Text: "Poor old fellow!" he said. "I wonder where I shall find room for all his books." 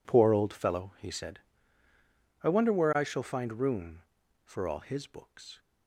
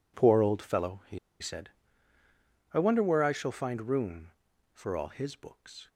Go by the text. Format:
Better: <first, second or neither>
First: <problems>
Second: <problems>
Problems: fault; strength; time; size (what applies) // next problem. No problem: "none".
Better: first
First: none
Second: pauses between "he" and "said"; slight; at 1.1 s; 0.21 s long